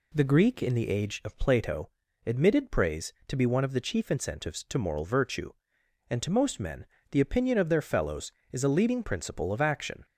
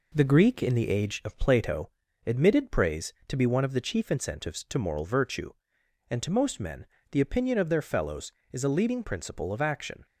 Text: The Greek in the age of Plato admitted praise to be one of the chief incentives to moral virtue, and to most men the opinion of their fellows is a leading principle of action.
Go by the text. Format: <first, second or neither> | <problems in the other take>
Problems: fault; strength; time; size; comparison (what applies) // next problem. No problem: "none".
first | gets quieter; throughout; 3.5 dB // pauses between "Plato" and "admitted"; at 1.8 s; 0.38 s long; also in the first // pauses between "men" and "the"; slight; at 6.8 s; 0.26 s long; slight in the first